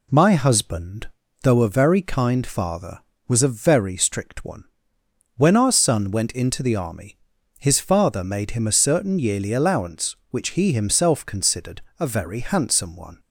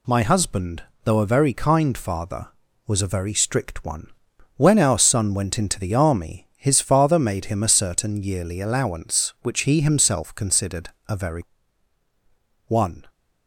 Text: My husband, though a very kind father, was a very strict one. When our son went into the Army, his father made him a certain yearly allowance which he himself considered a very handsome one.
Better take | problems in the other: first | pauses between "considered" and "a"; slight; at 10.8 s; 0.18 s long; slight in the first // skips "handsome"; at 12.0 s

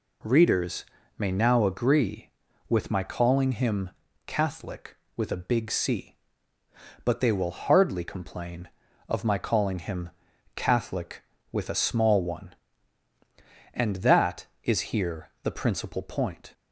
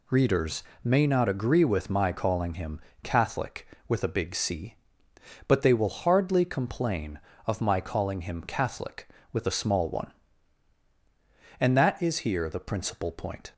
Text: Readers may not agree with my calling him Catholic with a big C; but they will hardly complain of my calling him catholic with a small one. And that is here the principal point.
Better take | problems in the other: second | pauses between "Readers" and "may"; slight; at 0.8 s; 0.32 s long; slight in the second // says "now" for "not"; at 1.3 s // pauses between "him" and "Catholic"; at 3.8 s; 0.38 s long; slight in the second // pauses between "him" and "catholic"; at 10.1 s; 0.44 s long

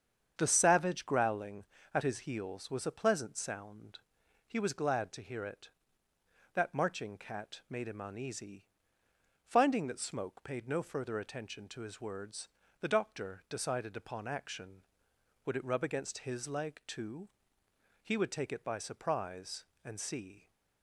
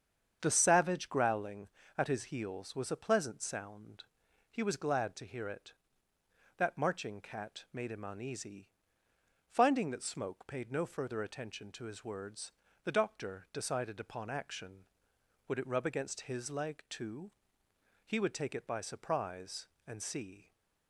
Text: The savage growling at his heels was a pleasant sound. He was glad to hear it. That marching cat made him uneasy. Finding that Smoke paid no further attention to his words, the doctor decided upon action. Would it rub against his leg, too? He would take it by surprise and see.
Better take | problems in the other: neither | starts louder than the rest; strong; the same in both

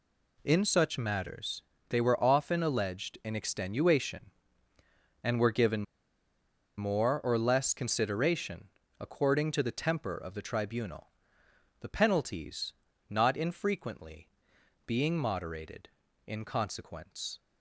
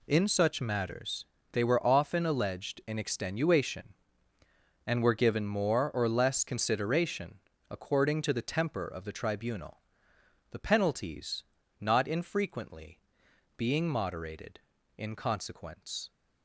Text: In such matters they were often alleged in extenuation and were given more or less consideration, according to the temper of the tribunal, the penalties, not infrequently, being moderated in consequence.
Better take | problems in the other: second | pauses between "matters" and "they"; slight; at 1.6 s; 0.26 s long; slight in the second // pauses between "given" and "more"; noticeable; at 5.8 s; 0.94 s long

